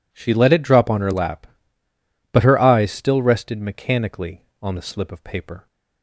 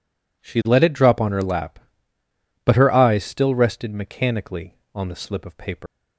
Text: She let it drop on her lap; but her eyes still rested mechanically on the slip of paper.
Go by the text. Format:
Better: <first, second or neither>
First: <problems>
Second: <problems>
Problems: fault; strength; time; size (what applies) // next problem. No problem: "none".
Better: first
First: none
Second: leaves "paper" unfinished; at 5.8 s; 140 ms